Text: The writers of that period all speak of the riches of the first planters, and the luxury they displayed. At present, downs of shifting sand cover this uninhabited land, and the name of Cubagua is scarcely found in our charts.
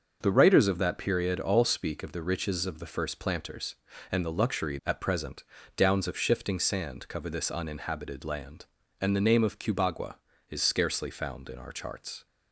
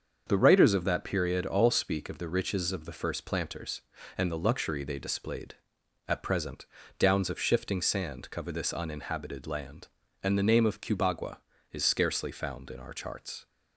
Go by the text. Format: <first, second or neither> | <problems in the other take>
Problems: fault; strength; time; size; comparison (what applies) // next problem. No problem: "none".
second | starts louder than the rest; noticeable; until 1.2 s; 6 dB; also in the second // skips "they displayed"; at 4.8 s